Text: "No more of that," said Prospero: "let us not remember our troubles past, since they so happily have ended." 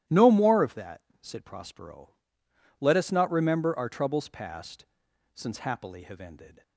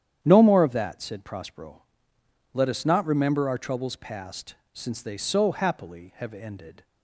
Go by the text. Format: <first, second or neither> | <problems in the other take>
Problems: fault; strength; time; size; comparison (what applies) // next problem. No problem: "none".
second | starts louder than the rest; strong; until 1.2 s; 13 dB; strong in the second // skips "they so"; at 5.5 s